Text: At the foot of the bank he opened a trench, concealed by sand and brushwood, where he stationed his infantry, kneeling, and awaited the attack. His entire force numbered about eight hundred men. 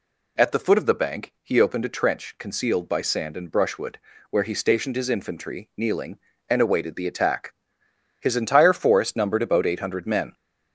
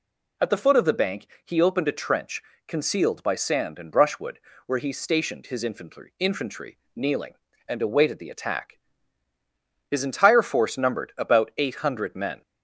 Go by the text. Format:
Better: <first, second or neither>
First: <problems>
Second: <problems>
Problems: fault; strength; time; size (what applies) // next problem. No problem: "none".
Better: first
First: none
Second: pauses between "bank" and "he"; slight; at 1.2 s; 0.18 s long // says "infantry" twice; at 6.1 s